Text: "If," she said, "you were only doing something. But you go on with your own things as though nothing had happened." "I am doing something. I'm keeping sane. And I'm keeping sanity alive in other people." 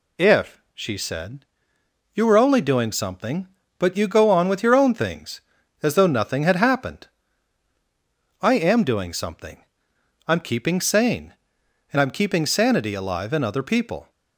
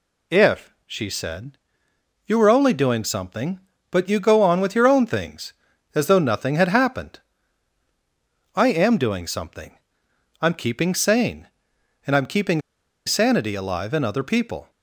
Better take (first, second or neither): first